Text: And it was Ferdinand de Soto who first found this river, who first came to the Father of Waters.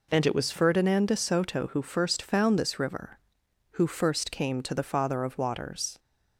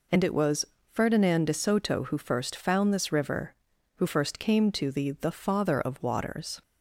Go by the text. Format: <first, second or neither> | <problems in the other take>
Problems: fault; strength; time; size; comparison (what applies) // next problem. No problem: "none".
first | pauses between "was" and "Ferdinand"; slight; at 0.6 s; 0.28 s long // says "the" twice; at 5.1 s